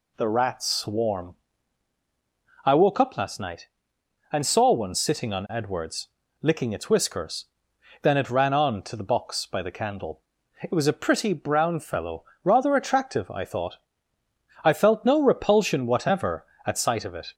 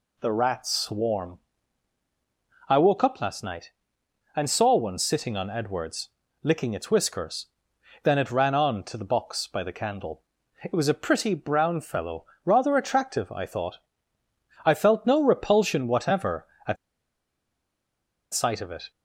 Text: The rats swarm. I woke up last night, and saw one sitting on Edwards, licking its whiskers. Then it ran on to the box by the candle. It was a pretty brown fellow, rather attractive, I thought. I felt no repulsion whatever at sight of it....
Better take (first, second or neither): first